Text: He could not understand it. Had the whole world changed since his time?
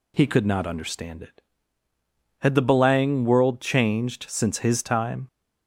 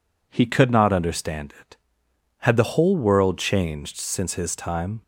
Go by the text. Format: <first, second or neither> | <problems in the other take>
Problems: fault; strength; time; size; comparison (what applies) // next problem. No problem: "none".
second | says "belang" for "whole"; at 2.6 s